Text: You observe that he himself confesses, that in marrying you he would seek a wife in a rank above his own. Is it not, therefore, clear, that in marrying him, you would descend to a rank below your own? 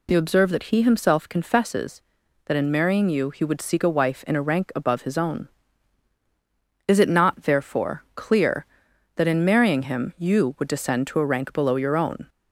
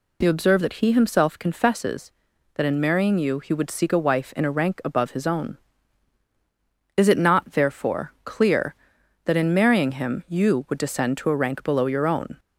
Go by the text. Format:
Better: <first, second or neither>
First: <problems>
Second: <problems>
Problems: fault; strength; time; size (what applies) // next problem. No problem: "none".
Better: neither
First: none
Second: none